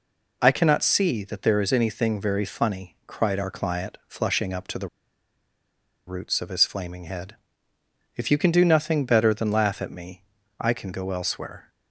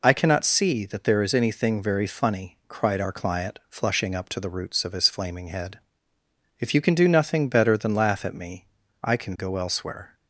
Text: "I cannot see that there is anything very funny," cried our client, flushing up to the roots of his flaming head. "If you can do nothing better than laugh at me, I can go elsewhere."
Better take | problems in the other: second | pauses between "the" and "roots"; at 4.8 s; 1.2 s long

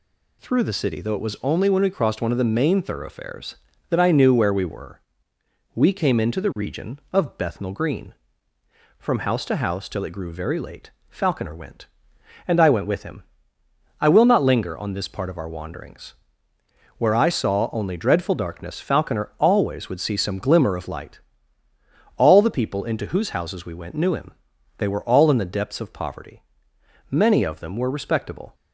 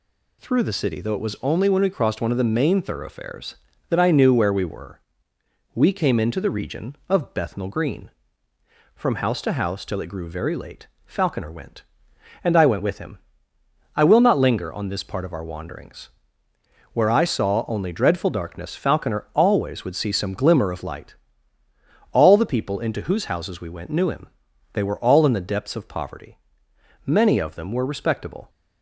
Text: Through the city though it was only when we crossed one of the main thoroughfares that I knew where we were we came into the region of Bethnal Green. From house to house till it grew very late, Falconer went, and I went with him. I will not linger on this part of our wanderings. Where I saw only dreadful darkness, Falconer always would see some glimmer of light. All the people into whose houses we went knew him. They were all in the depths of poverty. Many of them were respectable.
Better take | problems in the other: neither | pauses between "were" and "we"; noticeable; the same in both

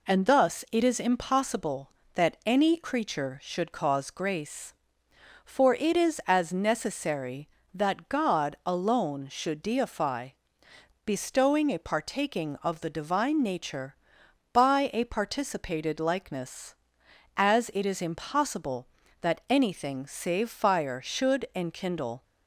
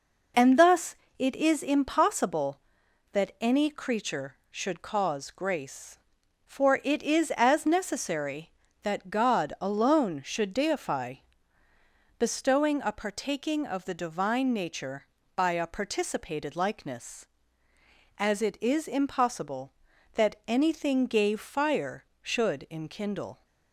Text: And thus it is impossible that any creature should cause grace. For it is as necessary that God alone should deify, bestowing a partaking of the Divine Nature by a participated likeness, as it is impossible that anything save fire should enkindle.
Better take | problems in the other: first | pauses between "thus" and "it"; slight; at 0.9 s; 0.22 s long // says "gave" for "save"; at 21.0 s

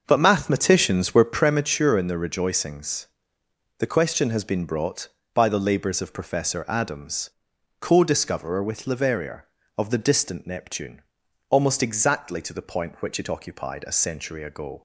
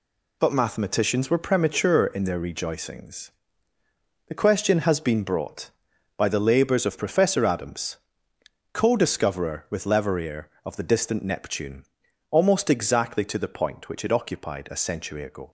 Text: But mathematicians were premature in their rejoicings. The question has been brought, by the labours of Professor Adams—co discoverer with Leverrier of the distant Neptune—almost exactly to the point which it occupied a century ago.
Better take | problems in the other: second | starts louder than the rest; until 1.6 s; 6.5 dB

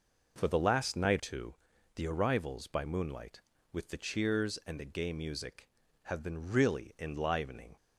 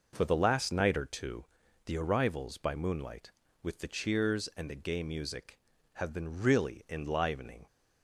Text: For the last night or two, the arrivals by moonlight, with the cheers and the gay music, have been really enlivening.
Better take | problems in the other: second | skips "or"; at 1.1 s

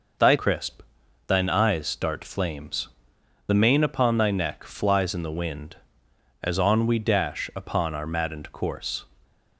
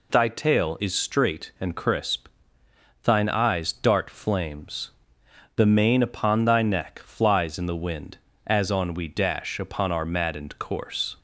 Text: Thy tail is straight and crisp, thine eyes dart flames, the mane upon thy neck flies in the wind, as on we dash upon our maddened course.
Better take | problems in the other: second | skips "tail is straight and"; at 0.3 s

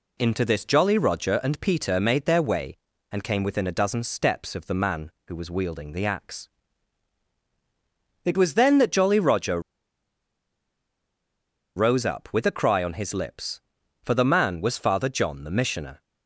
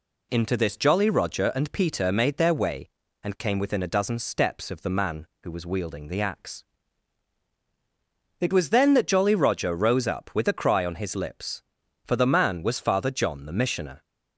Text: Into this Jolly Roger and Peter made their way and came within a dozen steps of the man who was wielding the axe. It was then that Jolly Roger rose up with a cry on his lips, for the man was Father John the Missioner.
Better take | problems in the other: second | pauses between "Roger" and "rose"; strong; at 9.5 s; 2.1 s long

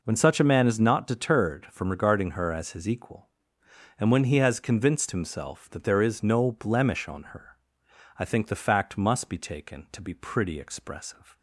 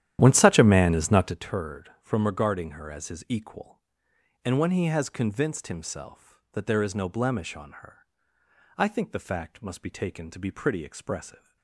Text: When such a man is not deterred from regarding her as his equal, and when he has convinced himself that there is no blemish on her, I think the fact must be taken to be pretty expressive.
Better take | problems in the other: first | starts louder than the rest; strong; until 1.4 s; 11.5 dB

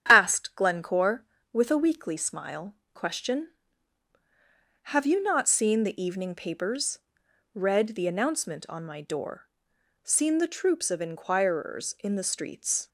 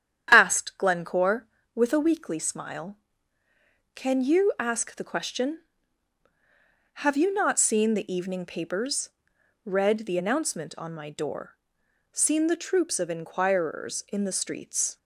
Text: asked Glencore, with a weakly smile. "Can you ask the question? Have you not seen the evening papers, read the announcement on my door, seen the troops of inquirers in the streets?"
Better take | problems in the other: second | starts louder than the rest; strong; until 1.0 s; 9.5 dB; strong in the second // skips "Can you ask the"; at 2.8 s

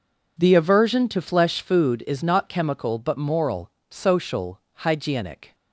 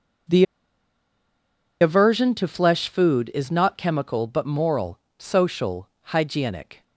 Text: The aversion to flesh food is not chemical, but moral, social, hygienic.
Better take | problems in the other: first | pauses between "The" and "aversion"; strong; at 0.4 s; 1.3 s long

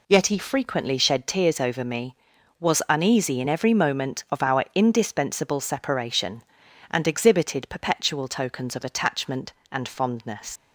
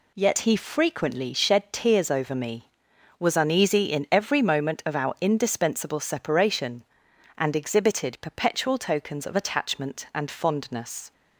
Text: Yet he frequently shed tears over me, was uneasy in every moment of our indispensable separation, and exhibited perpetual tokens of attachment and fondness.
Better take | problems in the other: second | leaves "fondness" unfinished; at 10.5 s; 100 ms

